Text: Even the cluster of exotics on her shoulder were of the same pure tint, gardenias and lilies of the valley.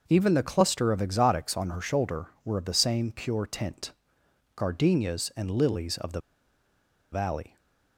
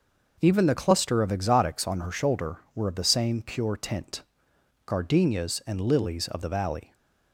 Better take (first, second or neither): second